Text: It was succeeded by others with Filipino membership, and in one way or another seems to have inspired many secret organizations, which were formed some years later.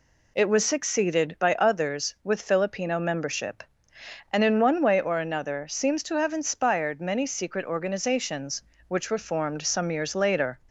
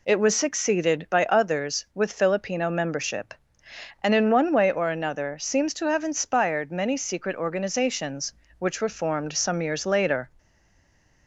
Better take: first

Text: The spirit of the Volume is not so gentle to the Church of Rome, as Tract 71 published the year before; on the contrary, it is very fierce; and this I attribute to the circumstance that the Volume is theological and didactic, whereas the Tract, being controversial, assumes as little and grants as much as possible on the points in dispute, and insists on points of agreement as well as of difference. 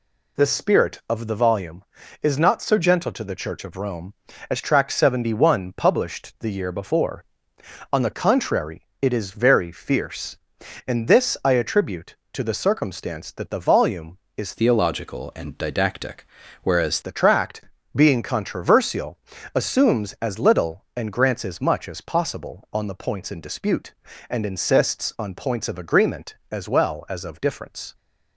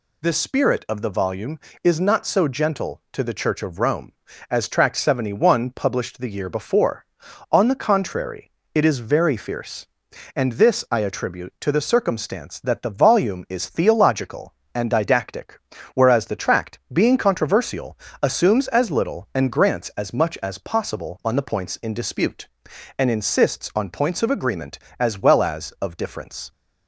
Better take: second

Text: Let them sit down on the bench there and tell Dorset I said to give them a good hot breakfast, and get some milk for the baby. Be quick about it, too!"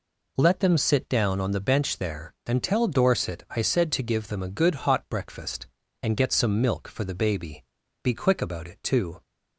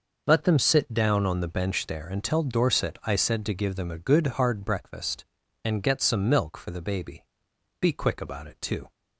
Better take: first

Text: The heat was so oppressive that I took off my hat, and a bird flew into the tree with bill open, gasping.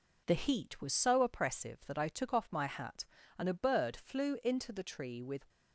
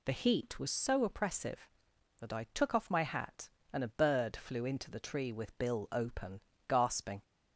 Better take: second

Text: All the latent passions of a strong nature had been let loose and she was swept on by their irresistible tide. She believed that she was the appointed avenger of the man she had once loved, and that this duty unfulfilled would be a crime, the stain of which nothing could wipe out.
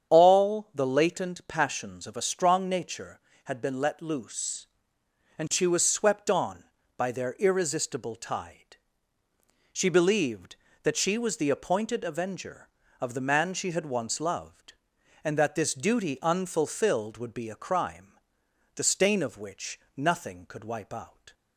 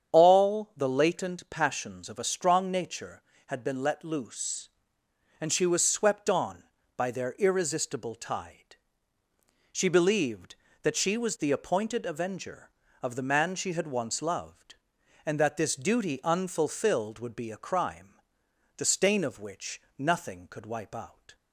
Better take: neither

